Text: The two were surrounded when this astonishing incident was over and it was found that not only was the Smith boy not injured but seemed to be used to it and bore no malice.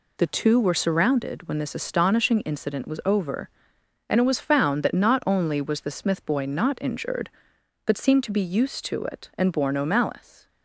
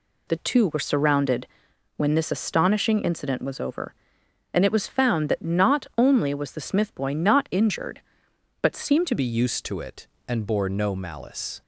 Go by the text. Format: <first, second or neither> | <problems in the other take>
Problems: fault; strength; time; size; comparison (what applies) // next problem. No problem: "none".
first | pauses between "surrounded" and "when"; noticeable; at 1.4 s; 0.50 s long // changes voice at "be"; from 9.1 s on; 2.5 s long